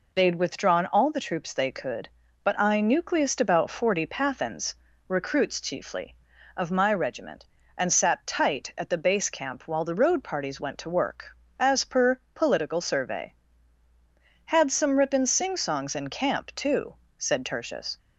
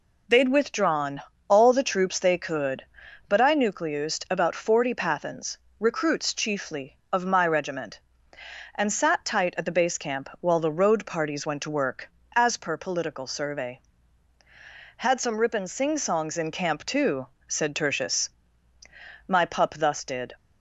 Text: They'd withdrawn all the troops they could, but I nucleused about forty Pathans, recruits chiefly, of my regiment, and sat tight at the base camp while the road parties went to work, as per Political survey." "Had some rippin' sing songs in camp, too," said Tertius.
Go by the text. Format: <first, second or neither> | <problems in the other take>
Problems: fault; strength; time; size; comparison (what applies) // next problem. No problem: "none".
first | pauses between "withdrawn" and "all"; slight; at 1.2 s; 0.24 s long // goes on to say "My pup thus did"; noticeable; from 19.2 s on; 1.0 s long